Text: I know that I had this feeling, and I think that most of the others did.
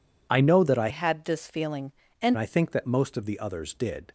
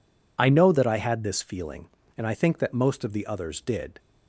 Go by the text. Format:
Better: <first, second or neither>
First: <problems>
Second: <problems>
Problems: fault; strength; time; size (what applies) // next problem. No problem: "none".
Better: second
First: changes voice from "had" to "and"; from 0.8 to 2.3 s; 1.5 s long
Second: none